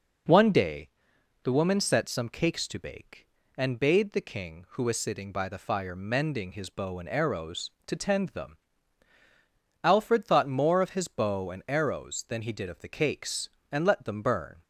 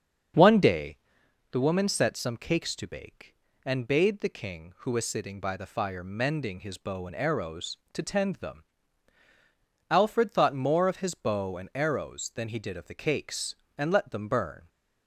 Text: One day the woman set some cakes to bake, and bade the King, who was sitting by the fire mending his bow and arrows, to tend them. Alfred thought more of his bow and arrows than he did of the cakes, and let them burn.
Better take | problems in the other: first | starts louder than the rest; strong; until 1.4 s; 7 dB // pauses between "day" and "the"; noticeable; at 0.9 s; 0.54 s long; noticeable in the first

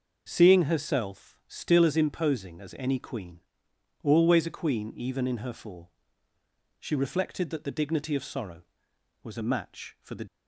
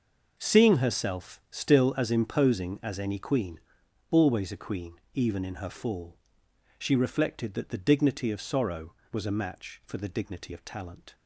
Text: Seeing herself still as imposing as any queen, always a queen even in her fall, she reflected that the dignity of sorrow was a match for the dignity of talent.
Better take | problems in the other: second | stops before "dignity of talent"; at 10.2 s

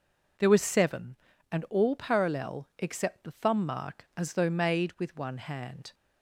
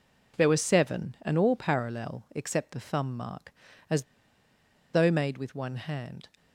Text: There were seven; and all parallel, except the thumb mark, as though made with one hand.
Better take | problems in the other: first | pauses between "as" and "though"; noticeable; at 4.0 s; 0.90 s long

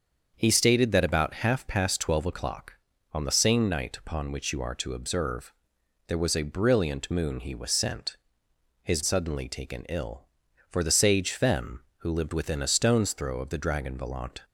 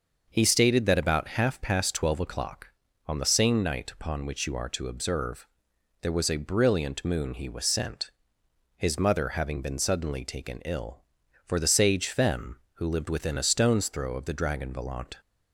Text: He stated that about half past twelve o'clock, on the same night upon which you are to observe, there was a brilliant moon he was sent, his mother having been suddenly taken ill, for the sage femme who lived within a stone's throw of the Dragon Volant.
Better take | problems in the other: second | starts louder than the rest; until 1.3 s; 7 dB; noticeable in the second // skips "mother having been"; at 9.0 s

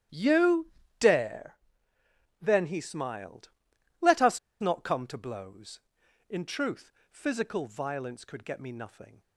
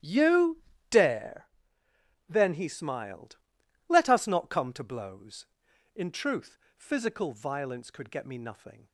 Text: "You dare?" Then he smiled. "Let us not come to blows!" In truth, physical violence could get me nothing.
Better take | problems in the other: second | starts louder than the rest; strong; until 1.4 s; 12 dB; strong in the second // pauses between "You" and "dare"; slight; at 0.6 s; 0.30 s long; slight in the second // pauses between "us" and "not"; slight; at 4.3 s; 0.22 s long

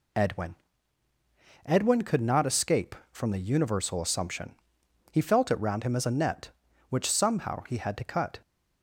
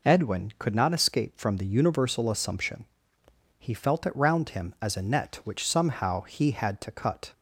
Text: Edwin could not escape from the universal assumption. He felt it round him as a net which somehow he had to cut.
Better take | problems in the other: second | says "Edwin" twice; at 1.6 s

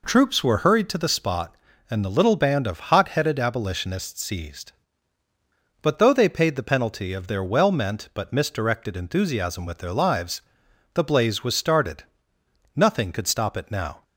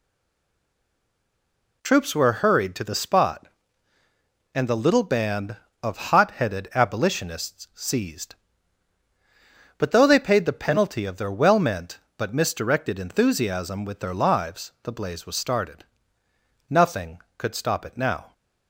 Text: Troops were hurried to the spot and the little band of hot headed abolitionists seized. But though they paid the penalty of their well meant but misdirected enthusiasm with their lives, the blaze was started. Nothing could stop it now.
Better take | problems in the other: first | stays silent before the first word; noticeable; until 1.8 s; 1.8 s long

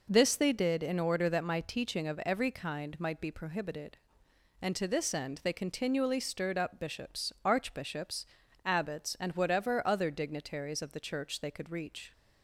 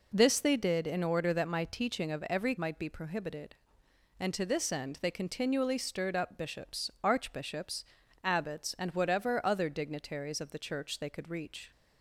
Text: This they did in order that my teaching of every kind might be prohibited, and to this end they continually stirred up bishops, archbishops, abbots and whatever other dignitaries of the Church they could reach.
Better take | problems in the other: first | skips "kind"; at 2.5 s

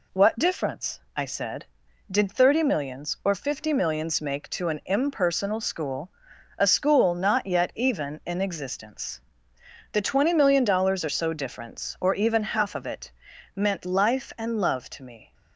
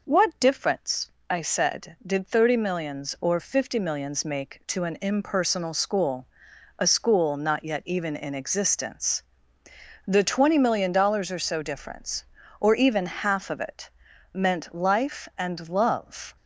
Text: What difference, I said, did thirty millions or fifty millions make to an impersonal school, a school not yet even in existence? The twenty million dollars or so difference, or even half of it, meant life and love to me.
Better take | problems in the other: first | stops before "to me"; at 16.3 s

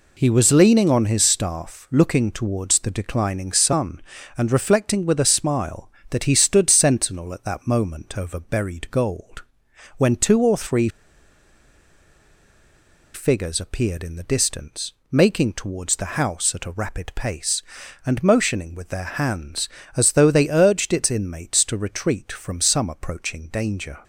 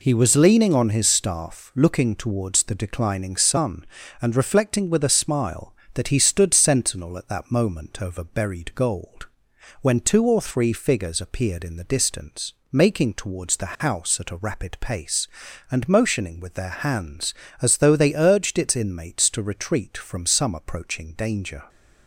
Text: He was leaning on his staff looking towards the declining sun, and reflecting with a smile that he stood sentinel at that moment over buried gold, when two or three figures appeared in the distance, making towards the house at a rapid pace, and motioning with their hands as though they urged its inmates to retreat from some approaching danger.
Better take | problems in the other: second | pauses between "three" and "figures"; strong; at 10.8 s; 2.2 s long

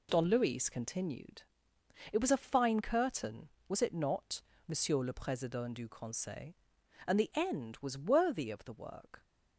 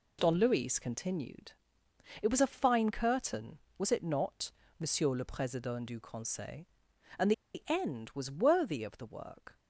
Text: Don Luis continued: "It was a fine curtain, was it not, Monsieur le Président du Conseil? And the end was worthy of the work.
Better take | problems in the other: first | pauses between "And" and "the"; slight; at 7.3 s; 0.23 s long

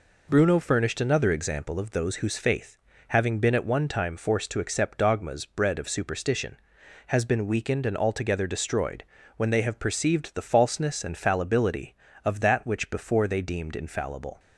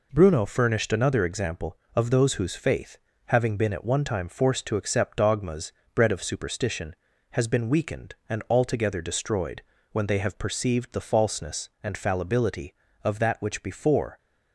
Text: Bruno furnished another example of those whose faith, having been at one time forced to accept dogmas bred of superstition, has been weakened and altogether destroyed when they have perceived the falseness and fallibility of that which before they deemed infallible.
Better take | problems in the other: first | pauses between "dogmas" and "bred"; slight; at 5.7 s; 0.22 s long // pauses between "destroyed" and "when"; slight; at 9.6 s; 0.30 s long; slight in the first // stops before "they deemed infallible"; at 14.1 s

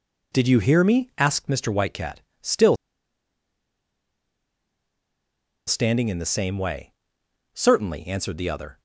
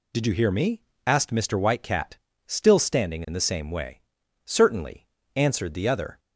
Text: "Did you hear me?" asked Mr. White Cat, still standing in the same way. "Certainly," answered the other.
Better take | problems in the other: second | pauses between "still" and "standing"; strong; at 2.7 s; 2.9 s long

